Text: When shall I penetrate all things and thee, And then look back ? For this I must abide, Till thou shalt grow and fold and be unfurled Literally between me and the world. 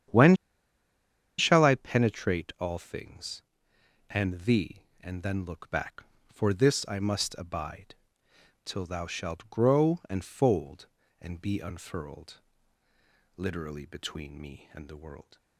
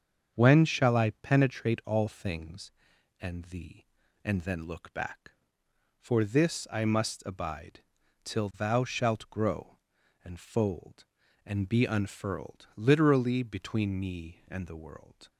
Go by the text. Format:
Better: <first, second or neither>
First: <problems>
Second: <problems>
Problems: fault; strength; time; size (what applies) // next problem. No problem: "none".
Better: second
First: starts louder than the rest; strong; until 2.1 s; 9 dB // pauses between "When" and "shall"; at 0.3 s; 1.0 s long // pauses between "unfurled" and "Literally"; noticeable; at 12.3 s; 0.96 s long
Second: starts louder than the rest; strong; until 1.3 s; 7 dB